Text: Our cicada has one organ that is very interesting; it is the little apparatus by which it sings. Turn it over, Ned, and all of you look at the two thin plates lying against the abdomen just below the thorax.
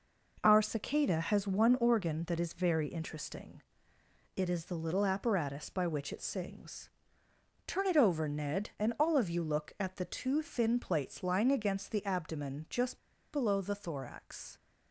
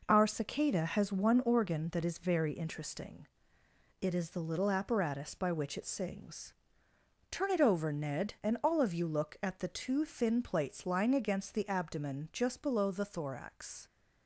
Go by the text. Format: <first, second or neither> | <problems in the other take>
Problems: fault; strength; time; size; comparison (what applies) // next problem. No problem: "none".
second | pauses between "just" and "below"; slight; at 12.9 s; 0.34 s long